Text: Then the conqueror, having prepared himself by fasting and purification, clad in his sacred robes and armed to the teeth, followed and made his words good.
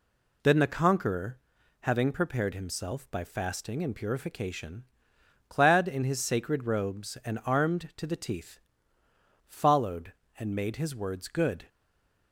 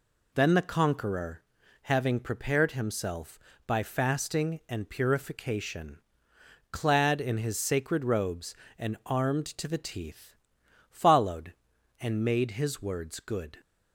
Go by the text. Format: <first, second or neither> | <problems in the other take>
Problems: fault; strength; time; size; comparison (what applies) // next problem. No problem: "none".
second | stays silent after the last word; slight; from 11.6 s on; 0.7 s long